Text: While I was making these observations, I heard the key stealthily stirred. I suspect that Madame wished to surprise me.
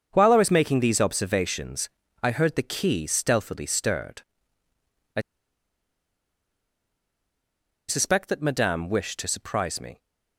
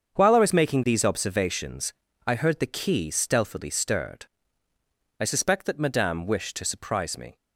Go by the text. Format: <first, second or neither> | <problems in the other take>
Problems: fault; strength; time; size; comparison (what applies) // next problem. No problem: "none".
second | starts louder than the rest; until 1.1 s; 7 dB; also in the second // pauses between "I" and "suspect"; strong; at 5.1 s; 2.6 s long